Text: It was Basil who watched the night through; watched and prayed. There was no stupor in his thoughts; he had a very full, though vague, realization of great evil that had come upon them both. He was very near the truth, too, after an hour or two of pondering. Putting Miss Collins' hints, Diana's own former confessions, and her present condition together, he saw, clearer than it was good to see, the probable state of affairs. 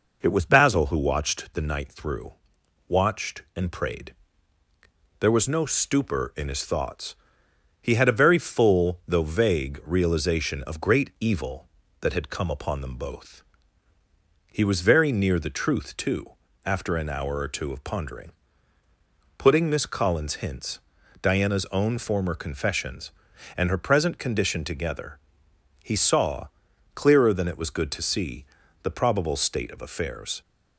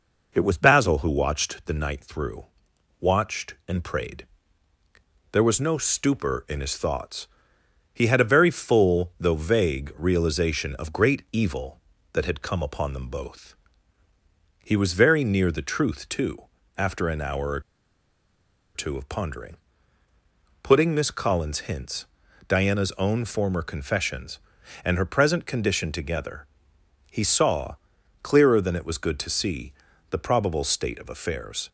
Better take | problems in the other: first | pauses between "or" and "two"; at 17.5 s; 1.1 s long

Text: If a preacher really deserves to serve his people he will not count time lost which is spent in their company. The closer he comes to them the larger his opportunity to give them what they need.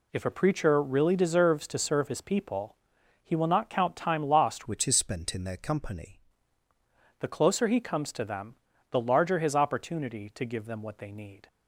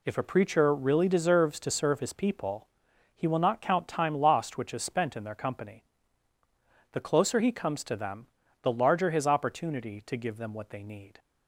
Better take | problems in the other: second | pauses between "people" and "he"; noticeable; at 2.7 s; 0.46 s long; noticeable in the second // changes voice from "which" to "company"; from 4.6 to 6.1 s; 1.5 s long // pauses between "them" and "the"; slight; at 8.5 s; 0.36 s long; slight in the second

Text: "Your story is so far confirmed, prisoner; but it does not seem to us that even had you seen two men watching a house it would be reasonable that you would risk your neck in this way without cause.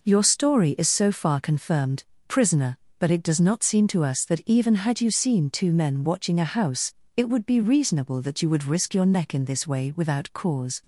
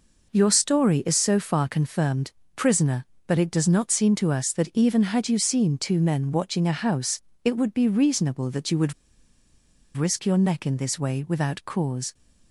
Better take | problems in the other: first | pauses between "house" and "it"; slight; at 7.2 s; 0.22 s long; slight in the first // pauses between "would" and "risk"; at 8.9 s; 1.0 s long

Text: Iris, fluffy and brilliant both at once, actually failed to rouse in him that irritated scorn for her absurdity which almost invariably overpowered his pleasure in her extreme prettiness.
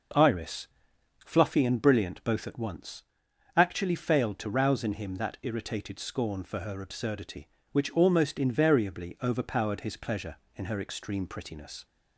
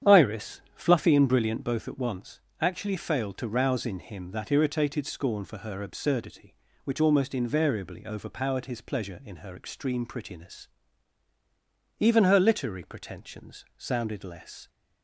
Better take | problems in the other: first | starts louder than the rest; strong; until 1.2 s; 9 dB // goes on to say "Even her literary pretensions sounded less"; strong; from 11.9 s on; 2.7 s long

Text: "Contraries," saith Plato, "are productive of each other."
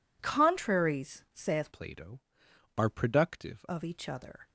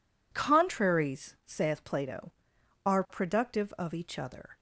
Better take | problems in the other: second | changes voice from "Plato" to "productive"; from 1.7 to 3.6 s; 1.9 s long

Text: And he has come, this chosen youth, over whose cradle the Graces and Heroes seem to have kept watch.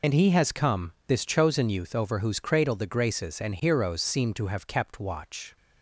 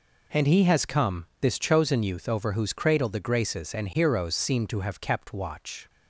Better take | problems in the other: second | loses the start of "And"; at 0.0 s; 70 ms

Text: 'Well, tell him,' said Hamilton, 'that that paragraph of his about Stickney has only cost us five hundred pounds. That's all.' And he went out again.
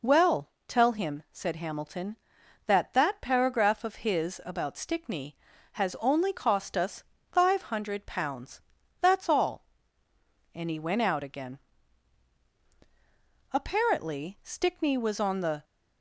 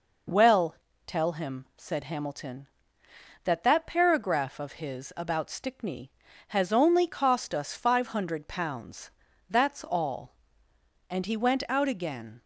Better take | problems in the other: second | pauses between "us" and "five"; slight; at 7.0 s; 0.28 s long // goes on to say "Apparently Stickney was on the"; strong; from 13.5 s on; 2.1 s long

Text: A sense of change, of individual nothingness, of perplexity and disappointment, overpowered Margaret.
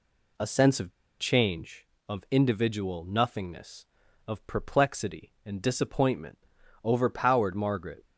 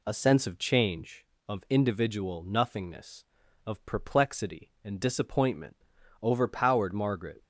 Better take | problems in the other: second | pauses between "of" and "change"; slight; at 0.9 s; 0.27 s long

